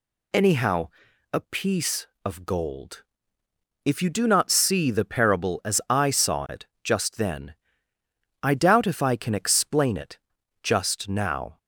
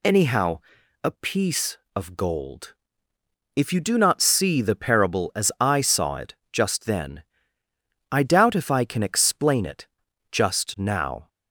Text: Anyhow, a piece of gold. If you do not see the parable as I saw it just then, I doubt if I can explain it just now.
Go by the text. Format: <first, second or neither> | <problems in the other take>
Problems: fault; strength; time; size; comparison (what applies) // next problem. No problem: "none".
neither | pauses between "it" and "just"; slight; the same in both // pauses between "it" and "just"; the same in both